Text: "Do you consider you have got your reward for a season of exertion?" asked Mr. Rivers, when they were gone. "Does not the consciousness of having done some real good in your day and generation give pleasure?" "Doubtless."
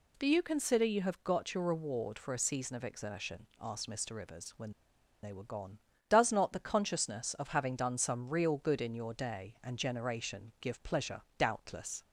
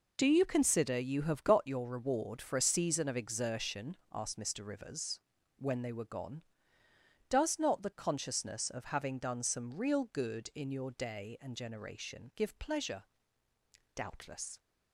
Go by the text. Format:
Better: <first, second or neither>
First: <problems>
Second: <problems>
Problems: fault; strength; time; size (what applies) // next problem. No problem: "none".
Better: second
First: pauses between "when" and "they"; noticeable; at 4.7 s; 0.51 s long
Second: none